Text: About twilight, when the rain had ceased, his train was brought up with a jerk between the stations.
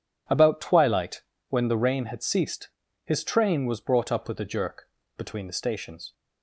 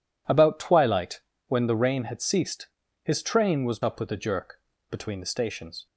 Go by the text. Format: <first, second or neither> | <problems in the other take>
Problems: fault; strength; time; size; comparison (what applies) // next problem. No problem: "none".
first | skips "brought"; at 3.8 s // pauses between "jerk" and "between"; slight; at 4.5 s; 0.30 s long; slight in the first